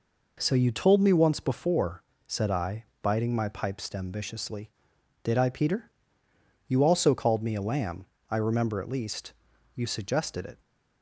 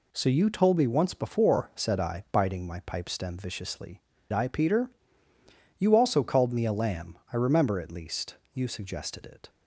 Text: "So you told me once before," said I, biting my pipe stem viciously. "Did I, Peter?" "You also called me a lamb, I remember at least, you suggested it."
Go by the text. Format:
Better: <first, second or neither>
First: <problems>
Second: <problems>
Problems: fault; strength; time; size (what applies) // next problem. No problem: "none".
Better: first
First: none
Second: skips "Did"; at 4.1 s